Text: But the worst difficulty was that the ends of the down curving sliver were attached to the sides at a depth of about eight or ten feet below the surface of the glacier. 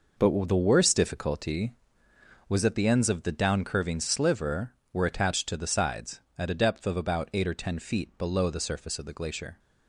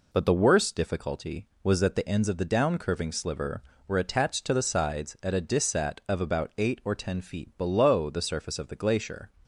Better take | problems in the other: first | says "dissat" for "depth"; at 5.4 s

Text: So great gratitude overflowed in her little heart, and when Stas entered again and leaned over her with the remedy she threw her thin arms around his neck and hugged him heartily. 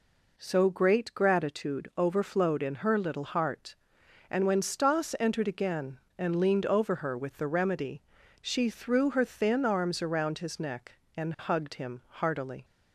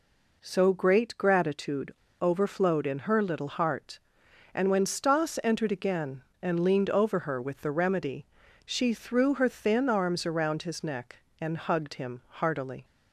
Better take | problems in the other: first | pauses between "gratitude" and "overflowed"; slight; at 1.9 s; 0.26 s long // pauses between "remedy" and "she"; at 8.2 s; 0.40 s long; also in the first

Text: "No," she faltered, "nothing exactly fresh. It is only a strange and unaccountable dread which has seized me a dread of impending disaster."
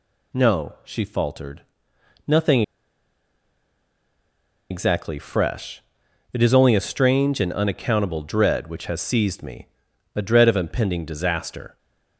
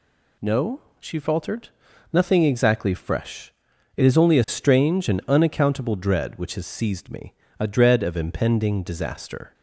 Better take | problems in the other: second | pauses between "nothing" and "exactly"; strong; at 2.6 s; 2.0 s long // pauses between "me" and "a"; noticeable; at 9.6 s; 0.46 s long; slight in the second

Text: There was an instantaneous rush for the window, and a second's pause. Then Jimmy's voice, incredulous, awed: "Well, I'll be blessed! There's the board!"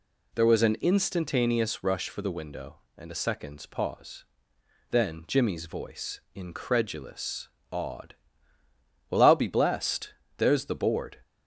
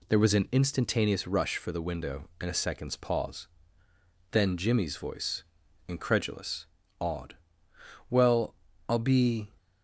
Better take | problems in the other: first | stops before "blessed There's the board"; at 9.5 s

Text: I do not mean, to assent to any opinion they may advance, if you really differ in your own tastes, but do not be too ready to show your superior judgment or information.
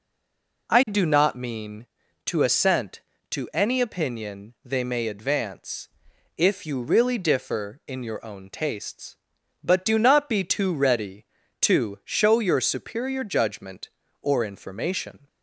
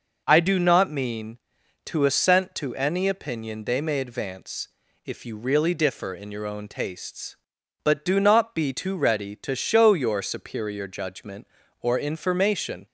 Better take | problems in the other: second | stays silent before the first word; slight; until 0.6 s; 0.6 s long

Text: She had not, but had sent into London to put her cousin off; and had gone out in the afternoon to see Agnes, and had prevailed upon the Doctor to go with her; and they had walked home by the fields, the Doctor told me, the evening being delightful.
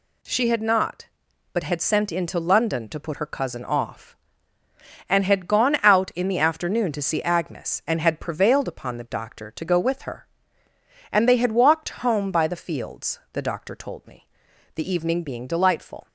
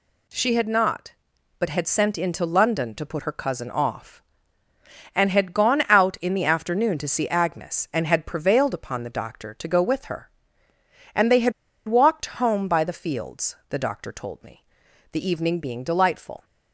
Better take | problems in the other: first | pauses between "had" and "walked"; slight; at 11.5 s; 0.35 s long

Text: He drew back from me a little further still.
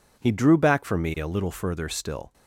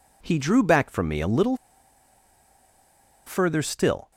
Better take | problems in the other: first | pauses between "little" and "further"; strong; at 1.5 s; 1.7 s long

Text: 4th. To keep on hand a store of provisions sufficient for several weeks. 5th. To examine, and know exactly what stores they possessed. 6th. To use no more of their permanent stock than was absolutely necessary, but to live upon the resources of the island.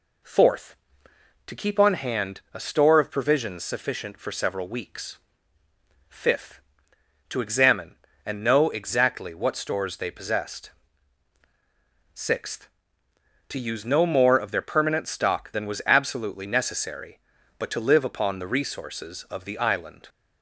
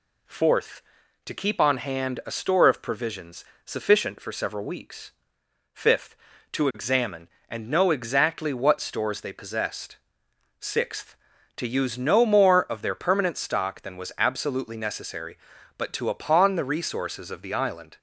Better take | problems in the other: first | pauses between "provisions" and "sufficient"; slight; at 3.4 s; 0.22 s long // skips "live"; at 16.0 s

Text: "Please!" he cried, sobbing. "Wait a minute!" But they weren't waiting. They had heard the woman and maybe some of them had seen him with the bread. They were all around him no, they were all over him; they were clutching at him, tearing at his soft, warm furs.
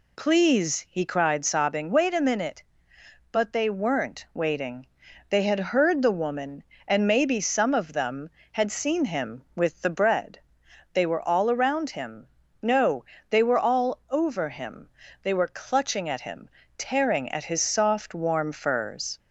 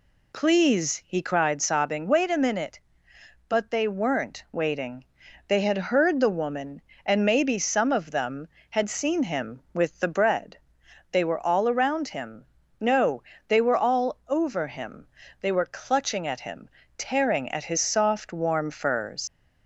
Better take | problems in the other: first | pauses between "him" and "no"; slight; at 12.4 s; 0.34 s long; slight in the first // leaves "furs" unfinished; at 19.2 s; 95 ms

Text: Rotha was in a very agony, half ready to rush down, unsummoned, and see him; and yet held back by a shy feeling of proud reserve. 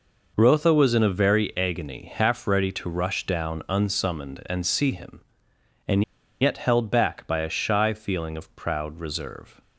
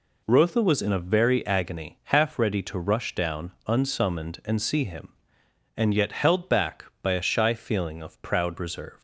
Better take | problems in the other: second | pauses between "and" and "yet"; at 6.0 s; 0.39 s long

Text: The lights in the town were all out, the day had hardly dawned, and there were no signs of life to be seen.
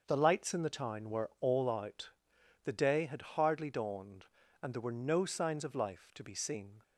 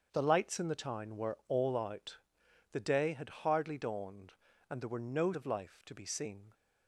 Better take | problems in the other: first | starts louder than the rest; until 1.1 s; 6.5 dB; noticeable in the first // skips "signs"; at 5.3 s

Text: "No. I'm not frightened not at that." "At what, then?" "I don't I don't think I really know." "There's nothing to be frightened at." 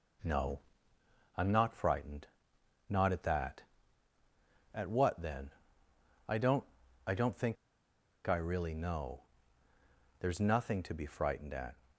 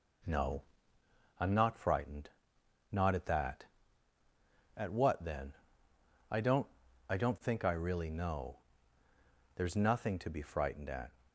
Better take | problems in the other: second | pauses between "frightened" and "not"; noticeable; at 2.2 s; 0.64 s long; noticeable in the second // pauses between "don't" and "I"; at 6.6 s; 0.42 s long; also in the second // pauses between "think" and "I"; noticeable; at 7.5 s; 0.71 s long

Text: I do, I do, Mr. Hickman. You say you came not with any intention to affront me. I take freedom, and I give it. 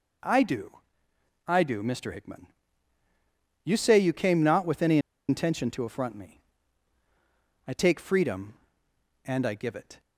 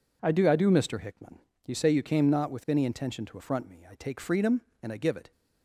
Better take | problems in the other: second | pauses between "any" and "intention"; slight; at 4.9 s; 0.30 s long

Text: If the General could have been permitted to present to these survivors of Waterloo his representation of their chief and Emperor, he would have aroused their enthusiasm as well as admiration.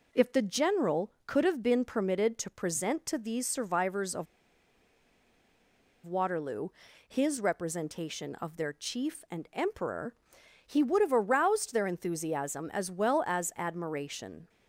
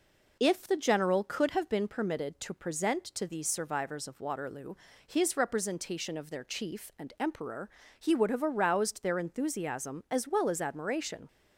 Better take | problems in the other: second | pauses between "of" and "Waterloo"; strong; at 4.2 s; 1.7 s long // pauses between "Waterloo" and "his"; at 6.6 s; 0.38 s long; slight in the second

